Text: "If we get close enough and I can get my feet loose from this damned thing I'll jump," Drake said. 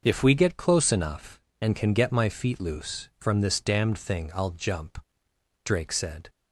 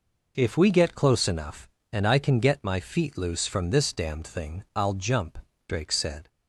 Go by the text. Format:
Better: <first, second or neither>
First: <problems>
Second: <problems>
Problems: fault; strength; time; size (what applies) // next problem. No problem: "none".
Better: second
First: starts louder than the rest; until 1.0 s; 6 dB // skips "I"; at 1.7 s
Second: none